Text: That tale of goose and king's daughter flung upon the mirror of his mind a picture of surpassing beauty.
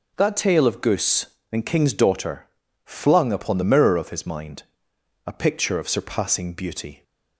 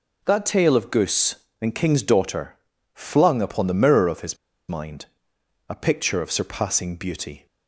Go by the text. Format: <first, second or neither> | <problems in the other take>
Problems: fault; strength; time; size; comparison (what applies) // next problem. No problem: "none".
first | pauses between "daughter" and "flung"; at 2.5 s; 0.40 s long; also in the first // pauses between "his" and "mind"; slight; at 4.3 s; 0.32 s long // pauses between "mind" and "a"; noticeable; at 5.0 s; 0.62 s long; noticeable in the first